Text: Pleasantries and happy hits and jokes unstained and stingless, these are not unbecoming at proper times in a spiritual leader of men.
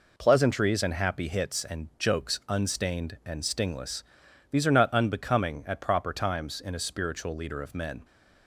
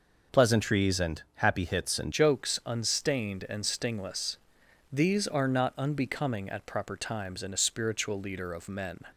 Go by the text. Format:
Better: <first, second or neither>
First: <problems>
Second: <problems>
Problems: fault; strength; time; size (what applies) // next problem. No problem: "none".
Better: first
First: none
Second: changes voice at "jokes"; from 2.1 s on; 6.8 s long